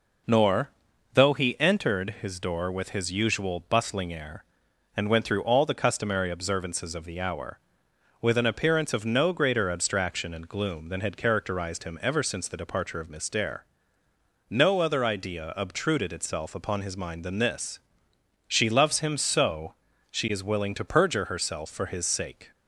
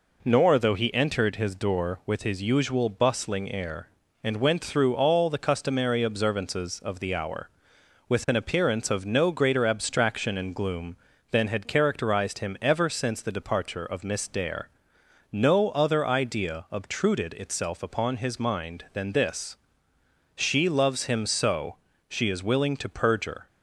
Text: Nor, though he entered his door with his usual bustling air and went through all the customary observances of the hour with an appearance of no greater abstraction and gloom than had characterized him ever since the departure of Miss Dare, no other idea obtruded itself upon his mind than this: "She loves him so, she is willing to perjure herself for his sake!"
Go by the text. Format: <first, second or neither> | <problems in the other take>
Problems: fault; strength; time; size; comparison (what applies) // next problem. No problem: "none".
first | stops before "herself for his sake"; at 23.4 s